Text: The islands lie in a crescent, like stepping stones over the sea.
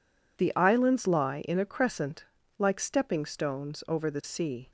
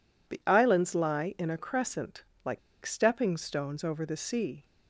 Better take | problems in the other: first | pauses between "like" and "stepping"; slight; at 2.5 s; 0.25 s long

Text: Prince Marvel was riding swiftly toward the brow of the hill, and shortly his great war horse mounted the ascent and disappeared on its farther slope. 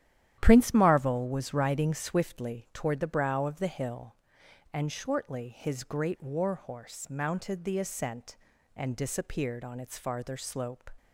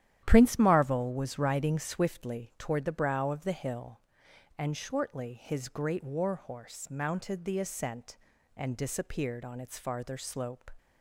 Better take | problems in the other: neither | starts louder than the rest; strong; the same in both

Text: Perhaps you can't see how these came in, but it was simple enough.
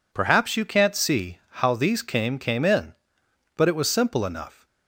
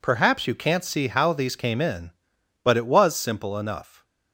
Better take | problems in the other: second | says "came" twice; at 2.3 s

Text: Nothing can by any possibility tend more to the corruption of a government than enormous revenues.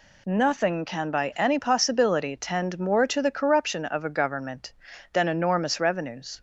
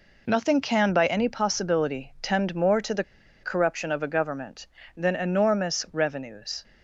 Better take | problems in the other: first | pauses between "the" and "corruption"; at 3.0 s; 0.39 s long

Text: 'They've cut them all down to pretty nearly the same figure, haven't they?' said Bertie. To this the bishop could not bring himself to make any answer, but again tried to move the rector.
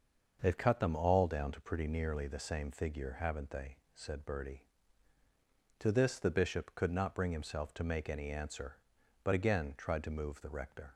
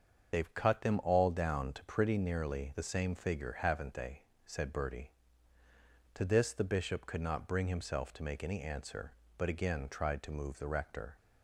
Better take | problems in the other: first | loses the start of "They've"; at 0.3 s; 45 ms // starts louder than the rest; until 1.3 s; 7 dB; also in the first

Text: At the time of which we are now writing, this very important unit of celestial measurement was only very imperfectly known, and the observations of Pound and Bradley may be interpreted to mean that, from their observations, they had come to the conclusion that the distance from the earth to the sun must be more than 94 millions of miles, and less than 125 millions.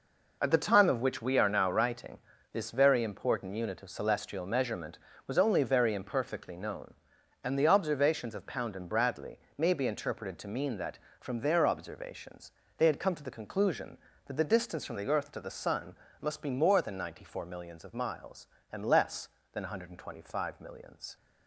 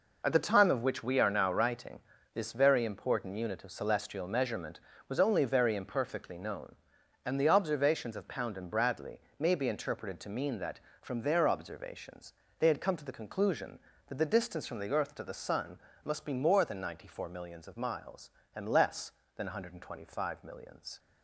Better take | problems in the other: neither | pauses between "Bradley" and "may"; slight; the same in both // pauses between "sun" and "must"; slight; the same in both

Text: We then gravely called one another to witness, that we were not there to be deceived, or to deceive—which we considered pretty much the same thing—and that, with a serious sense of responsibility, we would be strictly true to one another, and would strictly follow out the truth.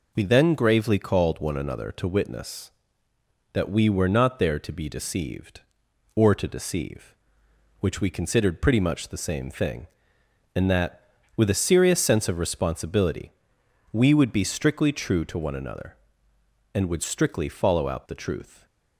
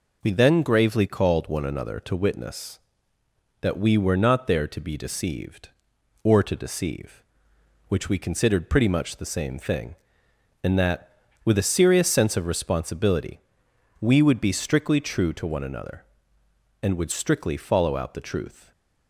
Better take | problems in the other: neither | none

